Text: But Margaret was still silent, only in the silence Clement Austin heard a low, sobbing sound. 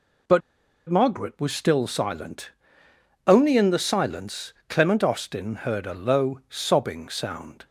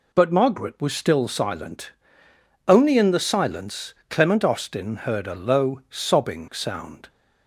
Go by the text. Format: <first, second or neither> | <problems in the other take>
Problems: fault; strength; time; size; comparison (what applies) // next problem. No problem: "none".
second | pauses between "But" and "Margaret"; noticeable; at 0.4 s; 0.48 s long // pauses between "silence" and "Clement"; slight; at 4.5 s; 0.16 s long; slight in the second